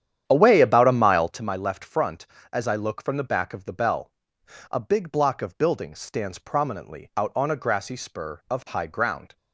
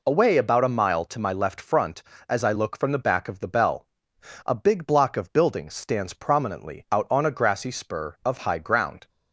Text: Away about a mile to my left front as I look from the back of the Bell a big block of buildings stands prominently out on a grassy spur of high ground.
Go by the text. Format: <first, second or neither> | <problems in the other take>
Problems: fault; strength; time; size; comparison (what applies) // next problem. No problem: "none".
second | starts louder than the rest; strong; until 1.5 s; 10 dB // pauses between "Bell" and "a"; noticeable; at 4.1 s; 0.60 s long; noticeable in the second